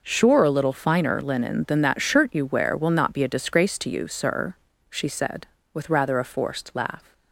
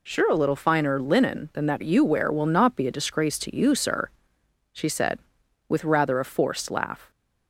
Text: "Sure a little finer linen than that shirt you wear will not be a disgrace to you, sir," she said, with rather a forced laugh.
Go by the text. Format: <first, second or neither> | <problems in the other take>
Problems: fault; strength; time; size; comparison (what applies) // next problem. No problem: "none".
first | skips "shirt"; at 1.8 s